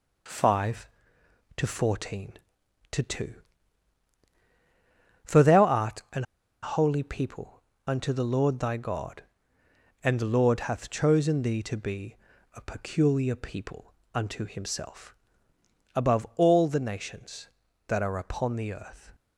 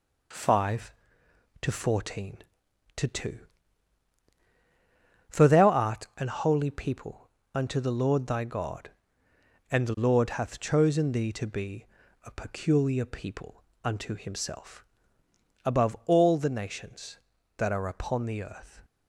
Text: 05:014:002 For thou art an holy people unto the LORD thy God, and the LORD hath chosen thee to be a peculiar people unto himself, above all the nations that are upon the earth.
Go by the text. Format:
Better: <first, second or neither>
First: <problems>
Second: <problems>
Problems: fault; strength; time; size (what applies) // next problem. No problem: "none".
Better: second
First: pauses between "an" and "holy"; at 6.2 s; 0.39 s long // pauses between "people" and "unto"; slight; at 7.6 s; 0.24 s long // pauses between "be" and "a"; at 12.1 s; 0.38 s long // pauses between "people" and "unto"; slight; at 13.9 s; 0.22 s long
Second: pauses between "people" and "unto"; slight; at 7.2 s; 0.24 s long // pauses between "be" and "a"; at 11.8 s; 0.38 s long // pauses between "people" and "unto"; slight; at 13.6 s; 0.22 s long